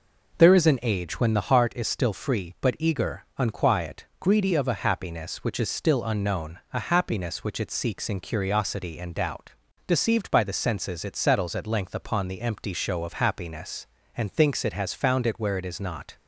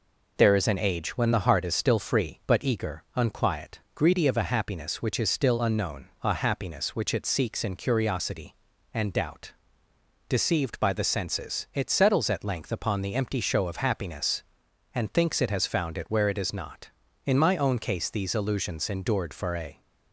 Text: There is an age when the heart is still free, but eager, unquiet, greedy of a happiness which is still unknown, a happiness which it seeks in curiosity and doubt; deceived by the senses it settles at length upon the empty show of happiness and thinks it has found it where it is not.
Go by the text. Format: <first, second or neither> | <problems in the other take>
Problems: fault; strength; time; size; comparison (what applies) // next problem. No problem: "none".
first | goes on to say "In my own case these illusions endured for a"; strong; from 17.2 s on; 2.5 s long